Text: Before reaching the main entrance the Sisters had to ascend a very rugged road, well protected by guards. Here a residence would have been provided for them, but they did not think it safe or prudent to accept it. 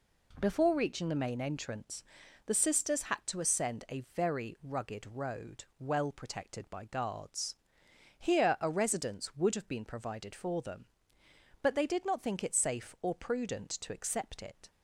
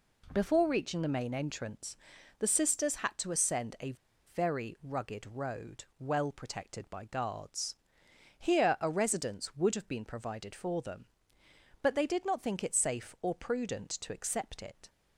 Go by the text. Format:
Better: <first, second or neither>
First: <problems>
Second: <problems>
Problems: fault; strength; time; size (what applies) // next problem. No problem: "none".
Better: first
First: pauses between "entrance" and "the"; at 2.0 s; 0.42 s long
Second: pauses between "entrance" and "the"; at 1.9 s; 0.42 s long // pauses between "a" and "very"; at 3.9 s; 0.40 s long